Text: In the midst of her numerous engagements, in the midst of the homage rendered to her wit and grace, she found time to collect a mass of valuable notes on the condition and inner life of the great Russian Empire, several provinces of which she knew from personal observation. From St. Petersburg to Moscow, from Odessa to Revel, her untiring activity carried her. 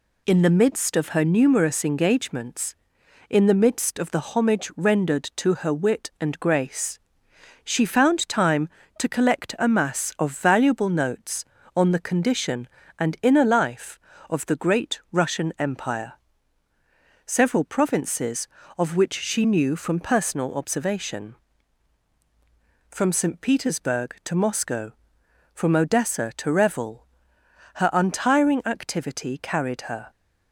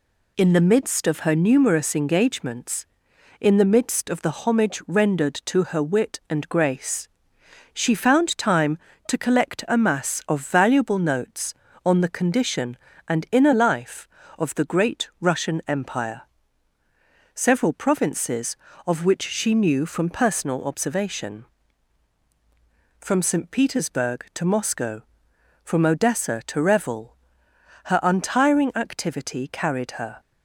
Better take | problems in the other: neither | none

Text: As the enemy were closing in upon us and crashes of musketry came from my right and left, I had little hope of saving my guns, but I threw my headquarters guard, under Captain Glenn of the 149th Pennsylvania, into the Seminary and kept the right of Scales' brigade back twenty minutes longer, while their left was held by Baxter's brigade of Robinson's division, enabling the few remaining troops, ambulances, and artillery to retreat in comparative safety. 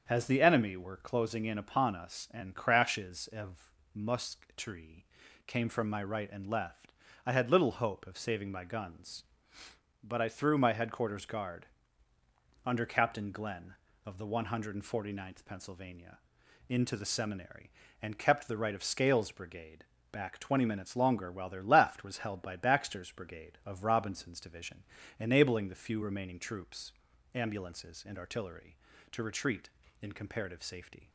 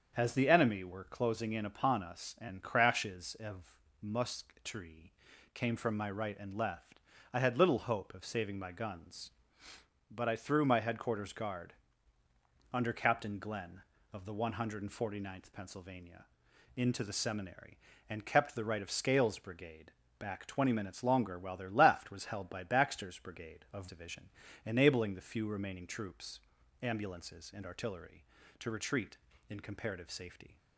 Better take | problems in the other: first | starts louder than the rest; until 1.1 s; 7 dB; also in the first // pauses between "of" and "musketry"; slight; at 3.7 s; 0.24 s long; slight in the first // pauses between "musketry" and "came"; at 5.1 s; 0.42 s long; also in the first // pauses between "brigade" and "back"; slight; at 19.9 s; 0.30 s long; slight in the first // skips "Robinson's"; at 23.8 s

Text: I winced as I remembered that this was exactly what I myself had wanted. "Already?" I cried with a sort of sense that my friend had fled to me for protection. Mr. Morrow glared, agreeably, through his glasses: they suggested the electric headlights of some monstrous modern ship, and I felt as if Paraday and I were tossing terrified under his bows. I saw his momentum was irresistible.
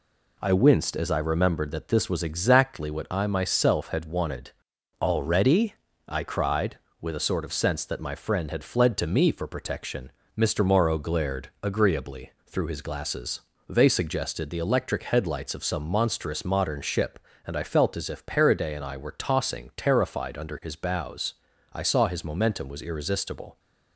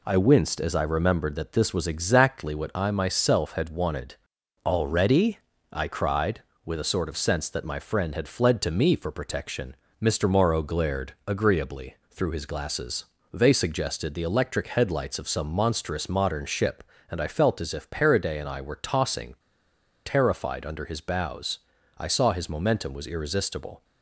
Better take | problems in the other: first | pauses between "tossing" and "terrified"; noticeable; at 19.3 s; 0.69 s long

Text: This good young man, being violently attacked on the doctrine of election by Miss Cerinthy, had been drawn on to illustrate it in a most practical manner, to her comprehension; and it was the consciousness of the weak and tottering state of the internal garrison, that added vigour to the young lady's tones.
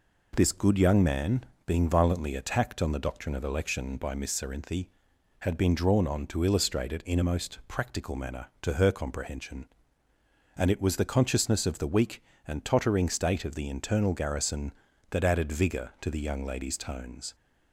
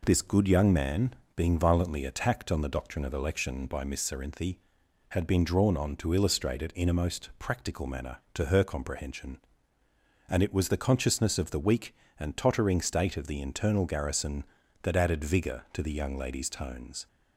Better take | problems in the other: neither | none

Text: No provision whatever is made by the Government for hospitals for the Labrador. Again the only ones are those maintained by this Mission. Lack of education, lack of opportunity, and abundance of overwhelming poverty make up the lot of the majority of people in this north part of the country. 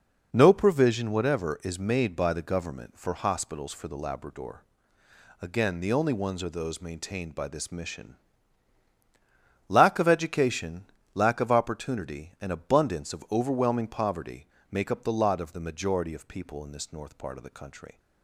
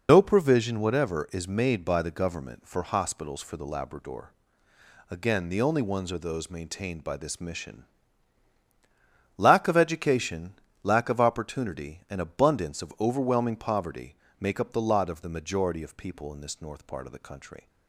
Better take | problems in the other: first | loses the start of "No"; at 0.0 s; 80 ms // pauses between "poverty" and "make"; slight; at 14.1 s; 0.24 s long; slight in the first

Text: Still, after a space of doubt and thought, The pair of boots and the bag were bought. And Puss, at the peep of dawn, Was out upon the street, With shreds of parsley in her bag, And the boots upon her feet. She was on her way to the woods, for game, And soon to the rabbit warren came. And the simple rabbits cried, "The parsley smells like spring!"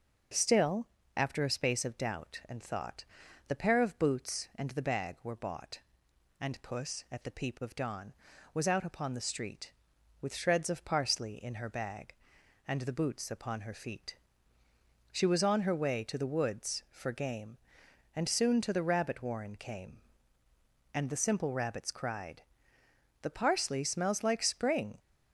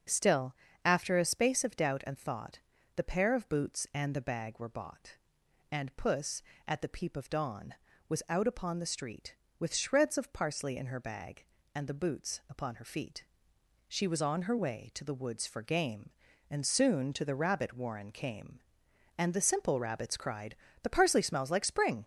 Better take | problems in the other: neither | starts louder than the rest; the same in both

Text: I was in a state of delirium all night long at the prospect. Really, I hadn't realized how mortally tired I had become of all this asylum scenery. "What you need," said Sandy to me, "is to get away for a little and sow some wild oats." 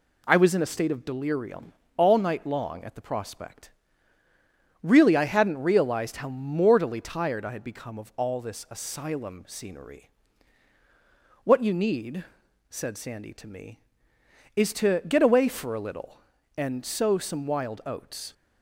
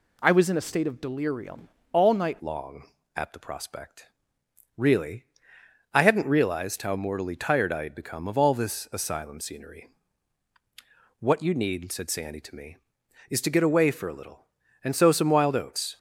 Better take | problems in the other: first | pauses between "delirium" and "all"; slight; at 1.6 s; 0.24 s long; slight in the first // changes voice at "long"; from 2.3 s on; 13.6 s long

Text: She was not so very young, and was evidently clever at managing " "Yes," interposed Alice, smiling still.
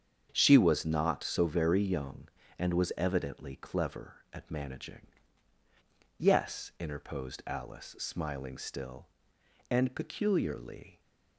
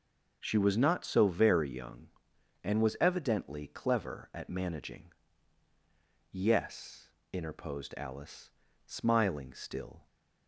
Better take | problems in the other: second | starts louder than the rest; strong; until 1.3 s; 8 dB; also in the second // goes on to say "And peculiarly"; noticeable; from 9.7 s on; 1.2 s long

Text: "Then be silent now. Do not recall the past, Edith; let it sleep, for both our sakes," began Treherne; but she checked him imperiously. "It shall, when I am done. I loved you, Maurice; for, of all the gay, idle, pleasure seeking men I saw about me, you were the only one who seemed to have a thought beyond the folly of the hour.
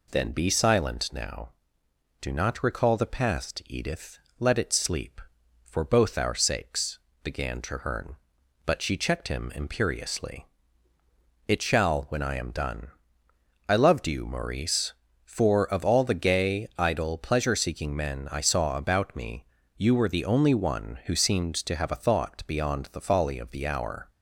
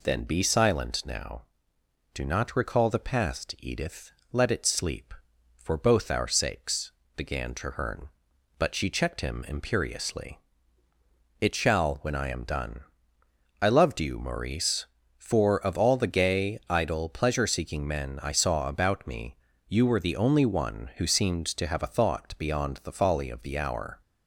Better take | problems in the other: neither | none

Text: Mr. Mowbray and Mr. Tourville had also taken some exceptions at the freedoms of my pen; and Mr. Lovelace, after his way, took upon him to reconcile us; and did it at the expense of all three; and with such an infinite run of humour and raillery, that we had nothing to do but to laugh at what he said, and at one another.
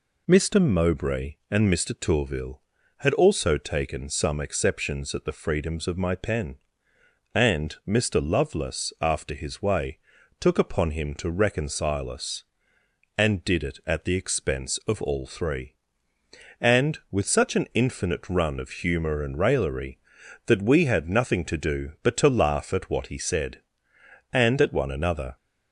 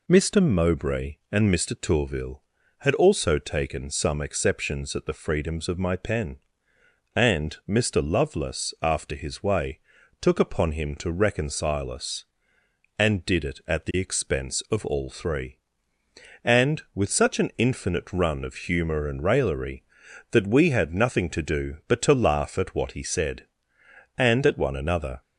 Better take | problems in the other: neither | none

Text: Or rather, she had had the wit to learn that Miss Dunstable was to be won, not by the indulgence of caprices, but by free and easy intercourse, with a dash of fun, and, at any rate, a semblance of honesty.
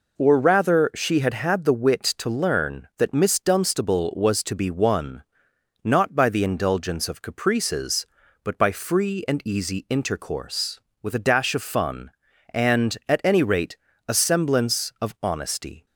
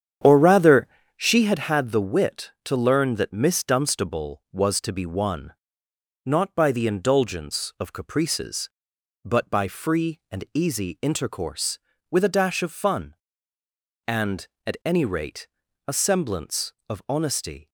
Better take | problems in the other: first | starts louder than the rest; strong; until 1.6 s; 8.5 dB

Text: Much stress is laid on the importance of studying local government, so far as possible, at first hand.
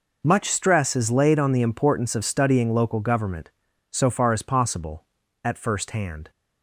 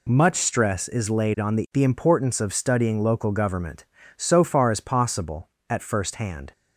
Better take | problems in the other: first | says "the" twice; at 1.7 s

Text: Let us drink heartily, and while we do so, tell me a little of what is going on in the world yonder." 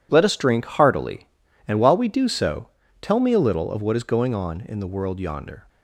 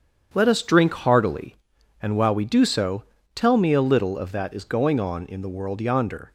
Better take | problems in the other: first | starts louder than the rest; strong; until 1.3 s; 8 dB // says "that" for "what"; at 4.3 s

